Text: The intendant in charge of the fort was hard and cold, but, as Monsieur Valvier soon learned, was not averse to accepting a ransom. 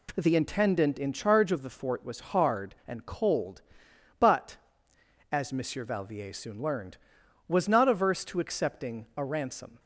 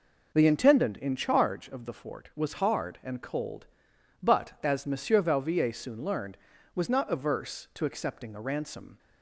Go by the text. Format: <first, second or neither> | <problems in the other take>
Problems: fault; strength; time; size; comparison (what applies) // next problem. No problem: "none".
neither | none